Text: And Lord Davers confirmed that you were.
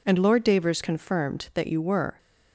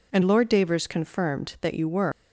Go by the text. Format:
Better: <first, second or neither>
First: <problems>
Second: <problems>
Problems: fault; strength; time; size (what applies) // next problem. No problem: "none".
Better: first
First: none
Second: leaves "were" unfinished; at 2.1 s; 125 ms